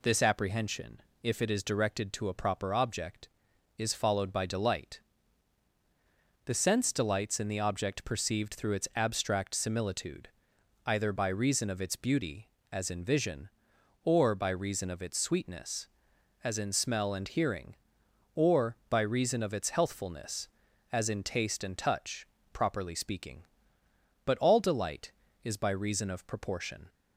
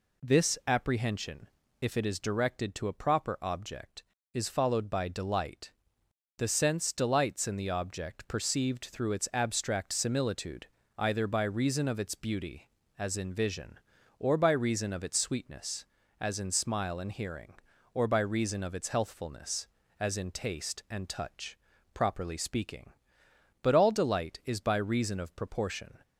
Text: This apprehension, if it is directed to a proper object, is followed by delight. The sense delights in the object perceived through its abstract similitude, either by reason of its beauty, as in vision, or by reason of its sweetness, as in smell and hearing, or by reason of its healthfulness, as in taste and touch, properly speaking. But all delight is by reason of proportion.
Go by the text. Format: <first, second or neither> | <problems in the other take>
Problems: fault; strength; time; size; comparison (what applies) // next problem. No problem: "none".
first | says "smile" for "smell"; at 16.4 s